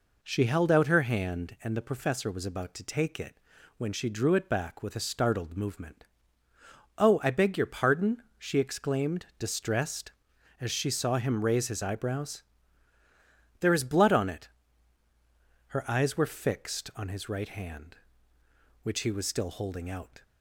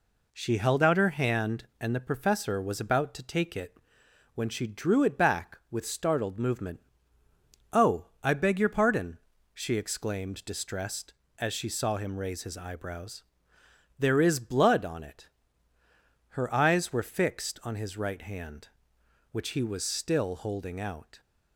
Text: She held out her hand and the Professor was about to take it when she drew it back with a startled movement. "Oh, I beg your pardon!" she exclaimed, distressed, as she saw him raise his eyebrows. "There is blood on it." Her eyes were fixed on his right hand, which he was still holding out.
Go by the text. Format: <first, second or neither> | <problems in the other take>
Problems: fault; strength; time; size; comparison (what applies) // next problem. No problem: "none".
first | pauses between "it" and "when"; noticeable; at 3.7 s; 0.58 s long; also in the first // skips "a"; at 5.8 s